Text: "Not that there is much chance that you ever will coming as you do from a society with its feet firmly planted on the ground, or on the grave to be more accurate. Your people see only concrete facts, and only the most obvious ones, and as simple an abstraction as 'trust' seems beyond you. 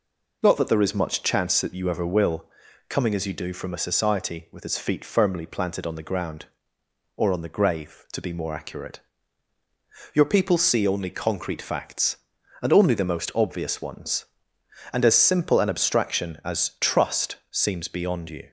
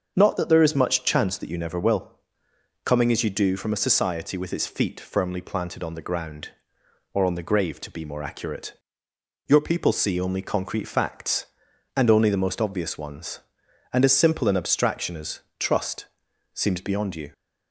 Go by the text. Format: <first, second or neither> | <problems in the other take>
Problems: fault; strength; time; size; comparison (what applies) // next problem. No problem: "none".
first | starts louder than the rest; until 1.1 s; 6.5 dB // says "never" for "ever"; at 1.5 s // pauses between "will" and "coming"; noticeable; at 2.1 s; 0.66 s long; also in the first // pauses between "as" and "trust"; slight; at 15.3 s; 0.20 s long // pauses between "trust" and "seems"; noticeable; at 16.0 s; 0.46 s long